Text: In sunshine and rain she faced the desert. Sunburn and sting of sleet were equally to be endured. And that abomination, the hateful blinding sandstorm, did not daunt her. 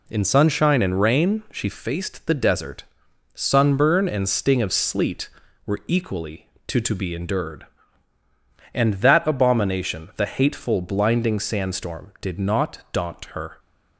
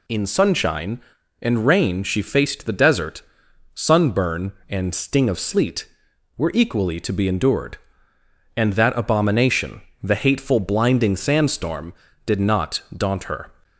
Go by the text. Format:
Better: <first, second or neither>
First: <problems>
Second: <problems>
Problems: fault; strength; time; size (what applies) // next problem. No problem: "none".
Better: second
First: says "to" twice; at 6.7 s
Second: none